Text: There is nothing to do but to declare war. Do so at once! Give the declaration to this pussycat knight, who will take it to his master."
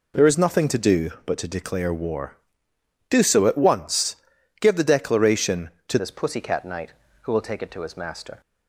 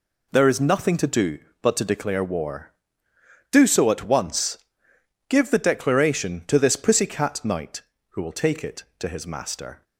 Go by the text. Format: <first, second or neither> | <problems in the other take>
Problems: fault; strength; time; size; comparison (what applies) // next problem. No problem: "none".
second | changes voice at "this"; from 5.9 s on; 2.5 s long